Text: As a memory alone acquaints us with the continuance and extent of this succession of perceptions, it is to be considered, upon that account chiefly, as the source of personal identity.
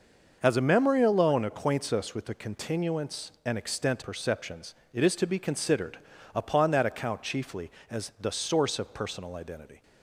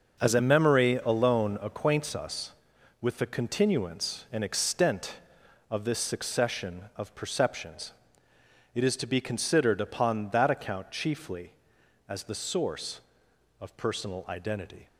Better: second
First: starts louder than the rest; noticeable; until 1.4 s; 6 dB // skips "of this succession of"; at 4.0 s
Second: starts louder than the rest; until 1.3 s; 6.5 dB

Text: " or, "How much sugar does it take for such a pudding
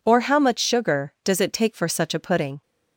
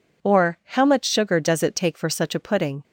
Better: neither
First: none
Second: none

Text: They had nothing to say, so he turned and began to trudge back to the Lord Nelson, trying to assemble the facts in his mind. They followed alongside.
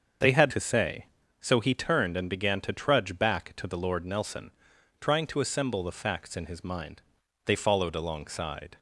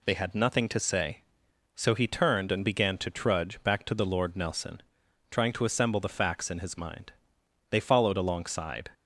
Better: second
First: starts louder than the rest; until 1.5 s; 7 dB // skips "nothing"; at 0.5 s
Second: none

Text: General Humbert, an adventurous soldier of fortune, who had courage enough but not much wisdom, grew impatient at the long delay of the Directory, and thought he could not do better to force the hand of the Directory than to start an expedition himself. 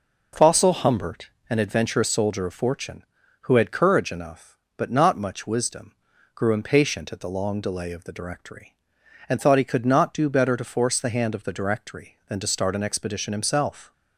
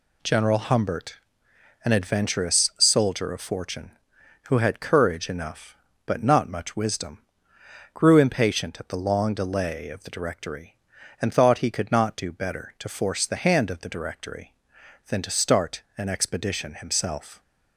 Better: second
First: says "Fossil" for "General"; at 0.3 s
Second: none

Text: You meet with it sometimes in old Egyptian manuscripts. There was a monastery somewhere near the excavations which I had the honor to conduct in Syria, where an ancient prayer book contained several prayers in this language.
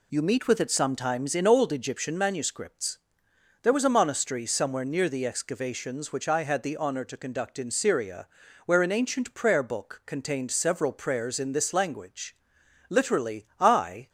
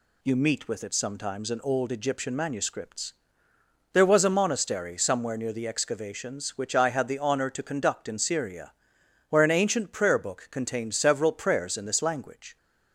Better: second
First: goes on to say "Literally I"; noticeable; from 12.8 s on; 1.2 s long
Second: none

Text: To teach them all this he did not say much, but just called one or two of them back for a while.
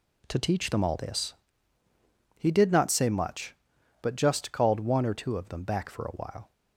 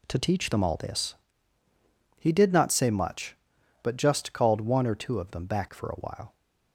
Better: neither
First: pauses between "this" and "he"; at 1.3 s; 1.0 s long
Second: pauses between "this" and "he"; at 1.1 s; 1.0 s long

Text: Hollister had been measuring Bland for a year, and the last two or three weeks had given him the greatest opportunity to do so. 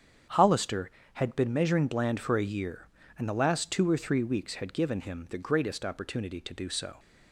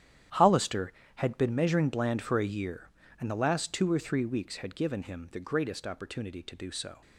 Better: first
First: starts louder than the rest; strong; until 1.5 s; 8 dB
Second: gets quieter; strong; throughout; 13.5 dB // starts louder than the rest; strong; until 1.5 s; 10.5 dB

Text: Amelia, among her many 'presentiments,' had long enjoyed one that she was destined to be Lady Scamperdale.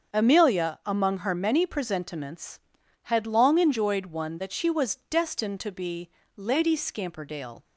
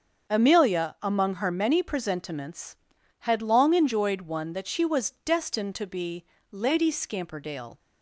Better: neither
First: starts louder than the rest; until 1.1 s; 6.5 dB // pauses between "be" and "Lady"; slight; at 6.0 s; 0.28 s long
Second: starts louder than the rest; until 1.3 s; 7 dB // pauses between "be" and "Lady"; slight; at 6.2 s; 0.28 s long

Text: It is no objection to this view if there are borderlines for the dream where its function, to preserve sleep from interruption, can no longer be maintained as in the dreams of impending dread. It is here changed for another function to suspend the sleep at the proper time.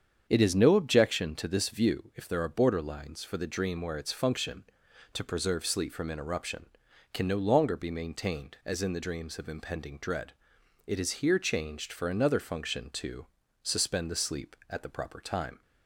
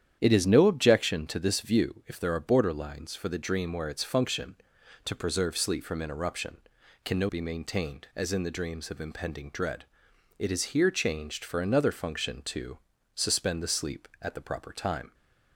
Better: first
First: starts louder than the rest; strong; until 1.2 s; 7.5 dB // pauses between "to" and "suspend"; at 13.2 s; 0.38 s long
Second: starts louder than the rest; strong; until 1.2 s; 9.5 dB // skips "longer"; at 7.2 s // pauses between "to" and "suspend"; at 12.7 s; 0.38 s long

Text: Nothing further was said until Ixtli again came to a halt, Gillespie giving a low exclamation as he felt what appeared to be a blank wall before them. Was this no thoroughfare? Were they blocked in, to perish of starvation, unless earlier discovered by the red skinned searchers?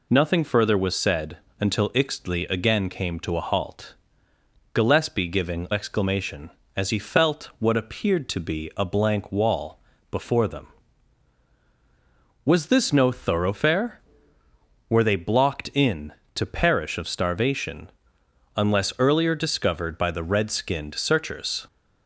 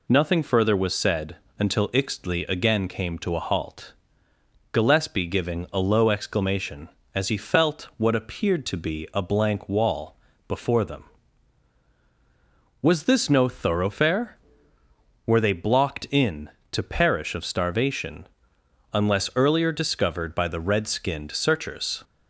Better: second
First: pauses between "said" and "until"; slight; at 1.3 s; 0.22 s long // skips "a low"; at 5.6 s // pauses between "wall" and "before"; slight; at 9.8 s; 0.30 s long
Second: pauses between "said" and "until"; slight; at 1.3 s; 0.22 s long // pauses between "wall" and "before"; slight; at 10.1 s; 0.30 s long

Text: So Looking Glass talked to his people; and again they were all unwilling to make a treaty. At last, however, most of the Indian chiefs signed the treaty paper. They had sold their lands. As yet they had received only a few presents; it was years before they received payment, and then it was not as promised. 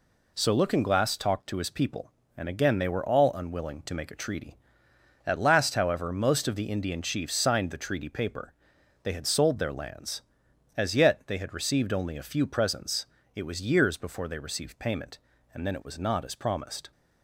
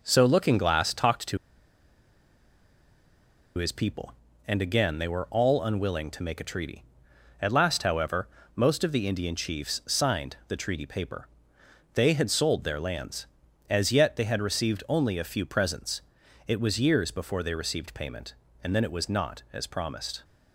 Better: first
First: none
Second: pauses between "to" and "his"; strong; at 1.3 s; 2.2 s long

